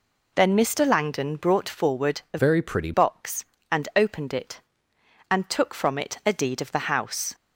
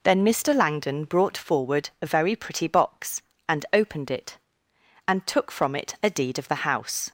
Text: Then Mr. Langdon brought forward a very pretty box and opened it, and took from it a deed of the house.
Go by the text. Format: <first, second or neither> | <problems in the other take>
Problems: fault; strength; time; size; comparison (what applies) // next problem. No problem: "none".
second | changes voice from "very" to "pretty"; from 2.3 to 2.9 s; 0.6 s long